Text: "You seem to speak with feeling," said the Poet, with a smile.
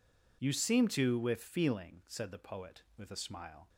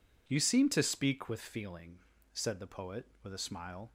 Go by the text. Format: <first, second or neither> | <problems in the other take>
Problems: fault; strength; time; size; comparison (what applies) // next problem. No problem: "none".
second | skips "speak"; at 1.1 s